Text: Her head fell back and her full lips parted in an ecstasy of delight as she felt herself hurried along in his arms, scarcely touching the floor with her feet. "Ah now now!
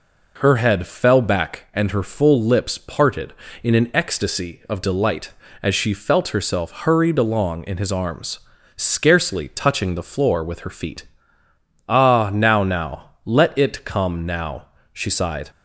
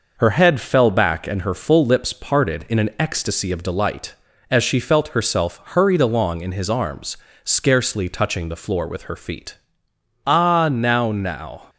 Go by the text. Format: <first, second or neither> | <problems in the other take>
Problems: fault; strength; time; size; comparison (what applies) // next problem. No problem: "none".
second | goes on to say "Let it come now she sighed"; strong; from 13.2 s on; 2.2 s long